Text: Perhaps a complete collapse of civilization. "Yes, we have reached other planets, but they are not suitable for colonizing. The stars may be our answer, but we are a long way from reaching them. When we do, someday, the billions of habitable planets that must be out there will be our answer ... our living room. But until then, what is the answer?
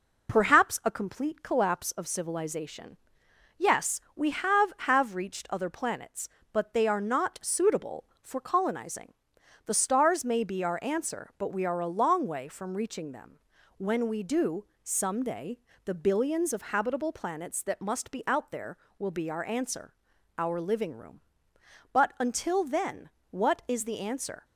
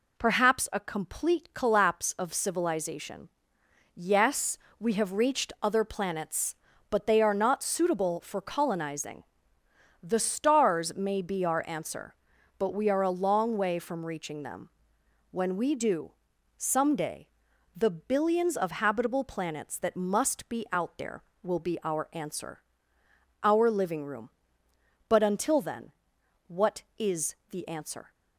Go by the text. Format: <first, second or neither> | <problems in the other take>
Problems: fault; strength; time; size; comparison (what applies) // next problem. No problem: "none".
second | says "have" twice; at 4.8 s